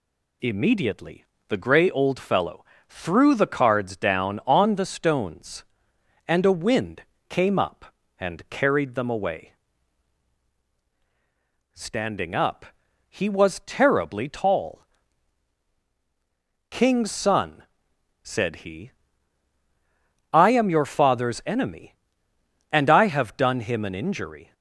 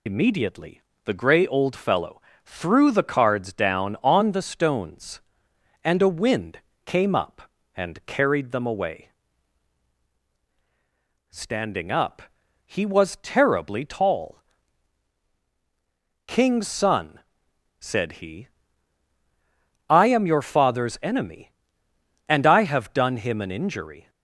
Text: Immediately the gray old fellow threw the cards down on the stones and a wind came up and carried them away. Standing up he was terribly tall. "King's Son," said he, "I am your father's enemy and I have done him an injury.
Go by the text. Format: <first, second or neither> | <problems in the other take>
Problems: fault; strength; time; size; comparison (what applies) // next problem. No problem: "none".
first | loses the start of "Immediately"; at 0.0 s; 85 ms // pauses between "Immediately" and "the"; slight; at 0.8 s; 0.24 s long; slight in the first // pauses between "fellow" and "threw"; slight; at 2.2 s; 0.24 s long; slight in the first // pauses between "wind" and "came"; slight; at 6.5 s; 0.26 s long; slight in the first // pauses between "up" and "he"; noticeable; at 12.2 s; 0.48 s long; noticeable in the first